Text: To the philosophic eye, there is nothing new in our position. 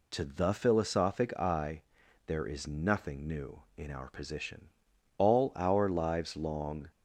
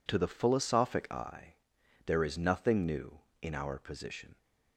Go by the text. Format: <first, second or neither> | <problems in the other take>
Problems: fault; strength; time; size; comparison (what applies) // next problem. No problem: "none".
second | goes on to say "All our lives long"; strong; from 5.1 s on; 1.7 s long